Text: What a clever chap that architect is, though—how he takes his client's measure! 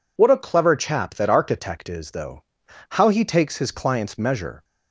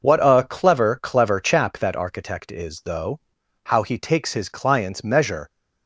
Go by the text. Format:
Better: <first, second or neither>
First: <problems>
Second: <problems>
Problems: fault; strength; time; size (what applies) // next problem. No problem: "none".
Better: first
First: none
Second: says "clever" twice; at 1.0 s